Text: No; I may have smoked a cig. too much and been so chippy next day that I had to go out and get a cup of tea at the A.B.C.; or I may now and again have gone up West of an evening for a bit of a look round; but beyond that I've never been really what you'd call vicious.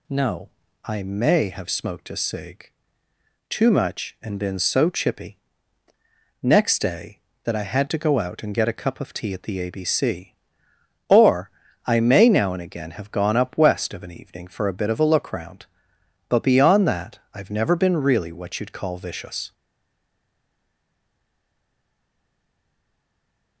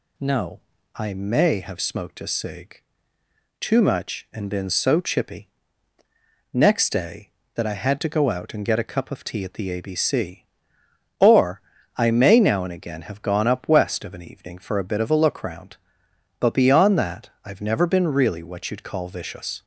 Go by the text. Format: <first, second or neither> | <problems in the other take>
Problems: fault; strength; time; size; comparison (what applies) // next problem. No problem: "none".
second | pauses between "chippy" and "next"; at 5.3 s; 1.0 s long; also in the second // pauses between "or" and "I"; at 11.4 s; 0.38 s long; also in the second // pauses between "that" and "I've"; slight; at 17.1 s; 0.16 s long; slight in the second // stays silent after the last word; strong; from 19.5 s on; 4.1 s long